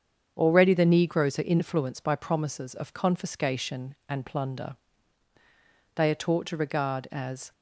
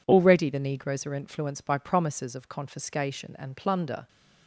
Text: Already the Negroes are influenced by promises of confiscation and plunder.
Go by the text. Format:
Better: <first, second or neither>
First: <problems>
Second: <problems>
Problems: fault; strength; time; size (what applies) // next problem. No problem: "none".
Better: second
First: starts louder than the rest; strong; until 1.3 s; 7.5 dB // goes on to say "They are taught to regard as"; from 5.9 s on; 1.5 s long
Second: none